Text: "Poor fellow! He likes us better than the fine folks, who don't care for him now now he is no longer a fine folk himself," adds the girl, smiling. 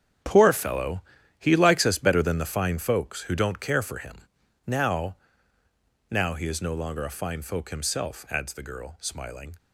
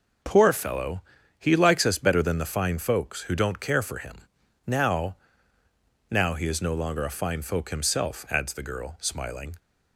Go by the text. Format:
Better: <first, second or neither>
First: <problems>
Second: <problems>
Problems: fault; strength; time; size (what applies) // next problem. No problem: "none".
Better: second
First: gets quieter; strong; throughout; 12 dB // pauses between "him" and "now"; noticeable; at 4.1 s; 0.46 s long // pauses between "now" and "now"; noticeable; at 5.1 s; 0.92 s long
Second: pauses between "him" and "now"; noticeable; at 4.1 s; 0.46 s long // pauses between "now" and "now"; noticeable; at 5.1 s; 0.92 s long